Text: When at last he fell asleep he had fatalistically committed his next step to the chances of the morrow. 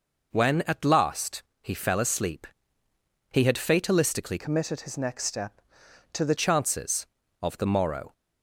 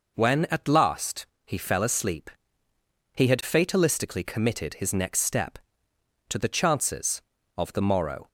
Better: second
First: pauses between "last" and "he"; slight; at 1.4 s; 0.18 s long // pauses between "asleep" and "he"; noticeable; at 2.4 s; 0.86 s long // changes voice from "committed" to "the"; from 4.3 to 6.3 s; 2.0 s long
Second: pauses between "last" and "he"; slight; at 1.2 s; 0.18 s long // pauses between "asleep" and "he"; noticeable; at 2.3 s; 0.86 s long

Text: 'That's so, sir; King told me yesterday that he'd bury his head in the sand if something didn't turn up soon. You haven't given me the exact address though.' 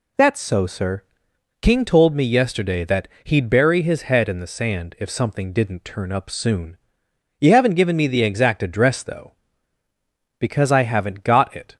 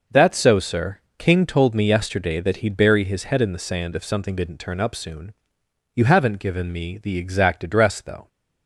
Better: second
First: pauses between "that" and "he'd"; slight; at 3.0 s; 0.16 s long // goes on to say "Because I haven't got it"; from 10.3 s on; 1.3 s long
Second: none

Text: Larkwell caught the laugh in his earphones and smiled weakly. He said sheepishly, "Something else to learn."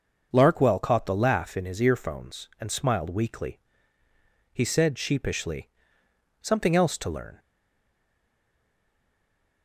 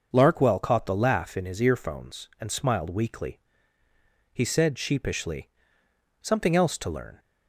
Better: second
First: starts louder than the rest; noticeable; until 1.3 s; 6 dB // stays silent after the last word; from 7.3 s on; 2.3 s long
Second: starts louder than the rest; noticeable; until 1.1 s; 6 dB

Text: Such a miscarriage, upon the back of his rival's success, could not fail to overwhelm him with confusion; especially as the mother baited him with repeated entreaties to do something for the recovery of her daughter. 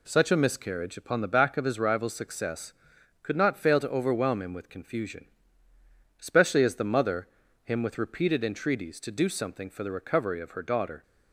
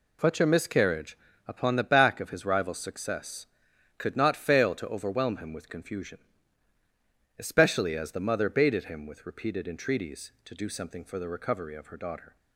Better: second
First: skips "baited"; at 7.4 s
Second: none

